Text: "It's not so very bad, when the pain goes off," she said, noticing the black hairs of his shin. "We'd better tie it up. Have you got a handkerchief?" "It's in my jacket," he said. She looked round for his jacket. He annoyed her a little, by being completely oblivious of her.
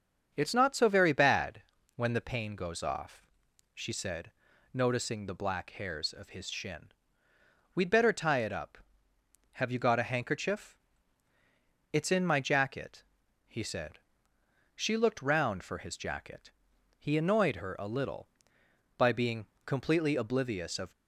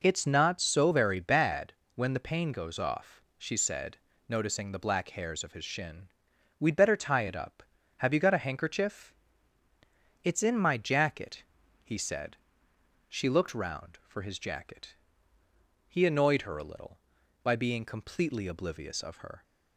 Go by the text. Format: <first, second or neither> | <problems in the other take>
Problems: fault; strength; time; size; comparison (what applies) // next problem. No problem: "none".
second | starts louder than the rest; until 1.3 s; 7 dB // pauses between "being" and "completely"; slight; at 19.4 s; 0.18 s long // stops before "her"; at 20.9 s